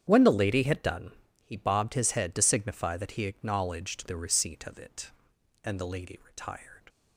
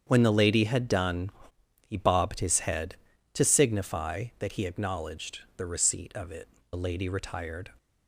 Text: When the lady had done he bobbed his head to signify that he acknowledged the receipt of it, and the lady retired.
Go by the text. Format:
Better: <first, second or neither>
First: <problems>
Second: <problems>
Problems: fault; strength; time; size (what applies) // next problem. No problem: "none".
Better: first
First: starts louder than the rest; strong; until 1.1 s; 8.5 dB // pauses between "done" and "he"; slight; at 1.1 s; 0.32 s long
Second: starts louder than the rest; strong; until 1.0 s; 7.5 dB // pauses between "done" and "he"; noticeable; at 1.3 s; 0.52 s long // pauses between "acknowledged" and "the"; slight; at 5.3 s; 0.18 s long // skips "and"; at 6.6 s